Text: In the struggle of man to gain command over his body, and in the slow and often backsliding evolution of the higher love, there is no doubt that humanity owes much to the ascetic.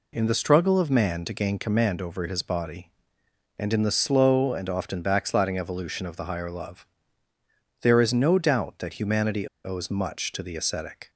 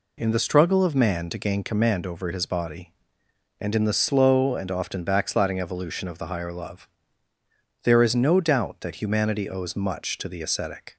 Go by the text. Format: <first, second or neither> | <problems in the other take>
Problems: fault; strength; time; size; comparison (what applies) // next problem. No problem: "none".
second | pauses between "humanity" and "owes"; slight; at 9.4 s; 0.16 s long